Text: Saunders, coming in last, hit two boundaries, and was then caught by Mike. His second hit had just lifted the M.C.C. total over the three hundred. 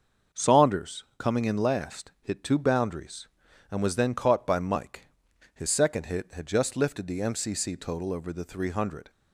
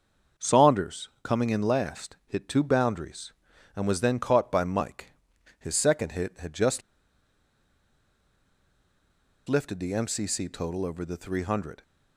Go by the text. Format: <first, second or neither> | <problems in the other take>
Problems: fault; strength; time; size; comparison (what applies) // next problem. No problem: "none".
first | starts louder than the rest; until 1.5 s; 6.5 dB; also in the first // pauses between "just" and "lifted"; strong; at 6.8 s; 2.6 s long